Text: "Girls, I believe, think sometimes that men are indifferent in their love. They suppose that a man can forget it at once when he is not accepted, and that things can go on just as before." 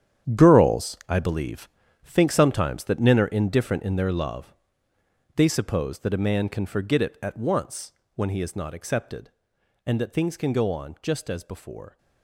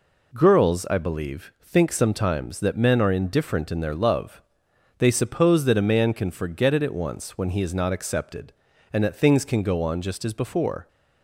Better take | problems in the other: second | gets quieter; strong; throughout; 11.5 dB // pauses between "once" and "when"; slight; at 7.9 s; 0.22 s long

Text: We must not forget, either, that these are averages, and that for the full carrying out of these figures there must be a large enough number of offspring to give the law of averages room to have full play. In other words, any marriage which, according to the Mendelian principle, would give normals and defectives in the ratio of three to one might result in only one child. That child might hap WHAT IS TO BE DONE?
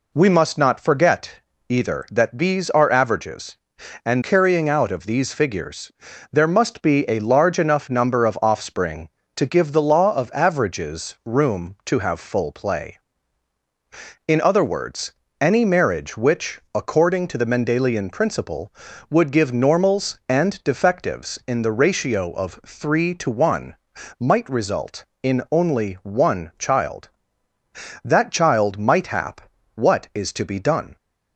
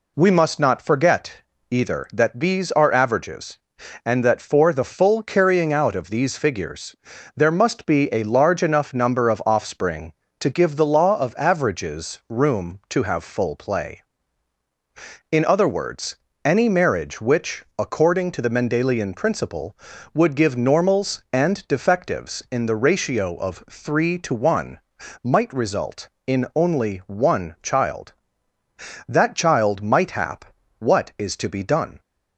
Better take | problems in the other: second | skips "that for the full"; at 4.2 s // pauses between "figures" and "there"; at 5.9 s; 0.40 s long; also in the second // pauses between "one" and "might"; noticeable; at 23.7 s; 0.46 s long; noticeable in the second // pauses between "hap" and "WHAT"; slight; at 29.4 s; 0.34 s long; slight in the second

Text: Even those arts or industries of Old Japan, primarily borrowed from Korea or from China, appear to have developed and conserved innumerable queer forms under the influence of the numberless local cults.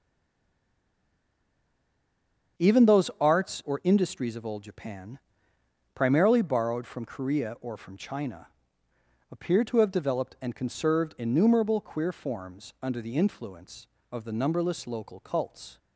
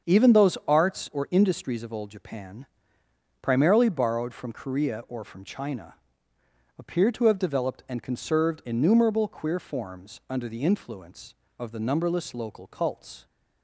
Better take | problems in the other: second | stays silent before the first word; strong; until 2.5 s; 2.5 s long // starts louder than the rest; until 3.7 s; 7 dB; also in the second

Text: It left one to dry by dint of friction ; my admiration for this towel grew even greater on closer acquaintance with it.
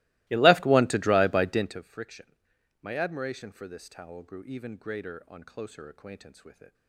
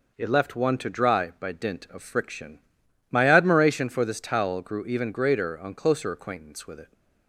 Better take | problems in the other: second | starts louder than the rest; strong; until 1.9 s; 22 dB

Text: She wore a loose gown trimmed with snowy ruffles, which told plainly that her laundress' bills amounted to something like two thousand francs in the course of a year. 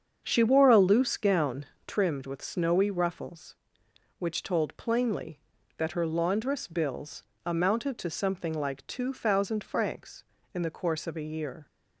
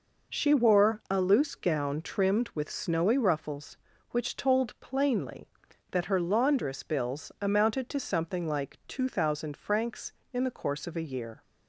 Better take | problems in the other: second | starts louder than the rest; strong; until 2.1 s; 7.5 dB // pauses between "gown" and "trimmed"; slight; at 1.6 s; 0.20 s long // pauses between "bills" and "amounted"; slight; at 7.2 s; 0.22 s long

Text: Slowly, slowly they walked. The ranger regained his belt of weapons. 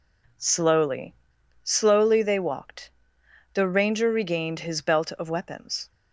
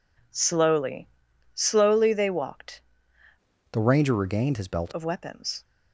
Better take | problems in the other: first | changes voice from "The" to "belt"; from 3.7 to 4.9 s; 1.2 s long

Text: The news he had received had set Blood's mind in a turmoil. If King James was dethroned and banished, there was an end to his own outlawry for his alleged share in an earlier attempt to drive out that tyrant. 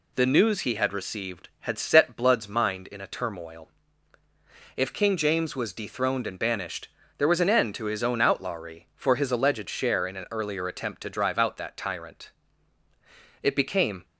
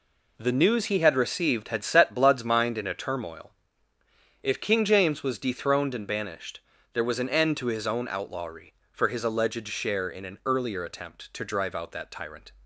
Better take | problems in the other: second | goes on to say "It became"; noticeable; from 13.4 s on; 0.62 s long

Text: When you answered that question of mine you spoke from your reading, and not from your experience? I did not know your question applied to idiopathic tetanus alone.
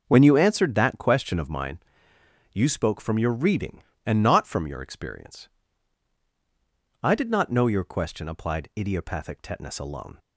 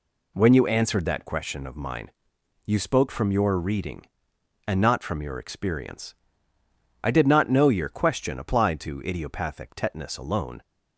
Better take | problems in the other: second | pauses between "mine" and "you"; noticeable; at 1.7 s; 0.78 s long; noticeable in the second // skips "to"; at 8.7 s

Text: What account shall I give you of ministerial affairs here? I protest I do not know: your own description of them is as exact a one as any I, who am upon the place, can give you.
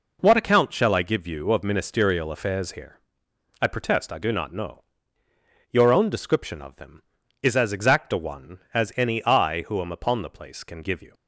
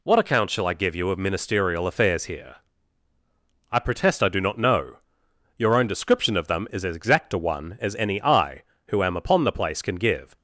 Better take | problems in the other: first | stops before "you"; at 10.3 s

